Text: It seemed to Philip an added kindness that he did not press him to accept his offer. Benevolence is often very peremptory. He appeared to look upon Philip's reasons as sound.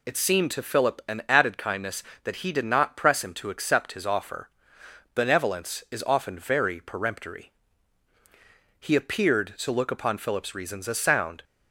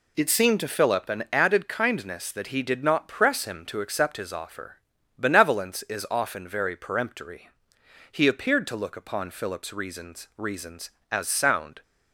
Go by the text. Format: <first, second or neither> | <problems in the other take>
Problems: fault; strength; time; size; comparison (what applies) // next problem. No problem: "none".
first | says "reasons" twice; at 10.3 s